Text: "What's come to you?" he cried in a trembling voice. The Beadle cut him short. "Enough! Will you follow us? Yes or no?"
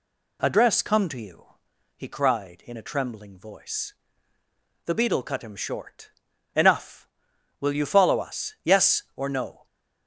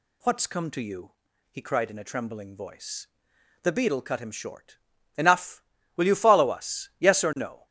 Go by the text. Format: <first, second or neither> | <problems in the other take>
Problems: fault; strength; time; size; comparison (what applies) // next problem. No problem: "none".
second | says "Address" for "What's"; at 0.4 s